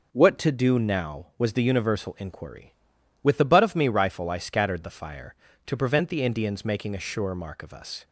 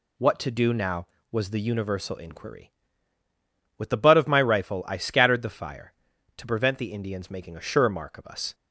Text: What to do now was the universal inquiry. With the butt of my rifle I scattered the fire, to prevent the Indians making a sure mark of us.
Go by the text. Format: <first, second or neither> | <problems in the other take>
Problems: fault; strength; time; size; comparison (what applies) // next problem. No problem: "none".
second | says "me" for "my"; at 3.7 s